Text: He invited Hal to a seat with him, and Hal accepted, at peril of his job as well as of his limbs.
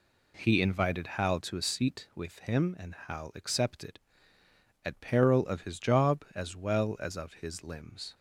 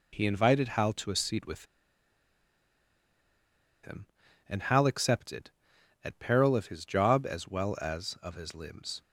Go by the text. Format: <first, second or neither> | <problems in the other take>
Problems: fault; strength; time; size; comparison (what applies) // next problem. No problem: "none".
first | pauses between "with" and "him"; strong; at 1.6 s; 2.1 s long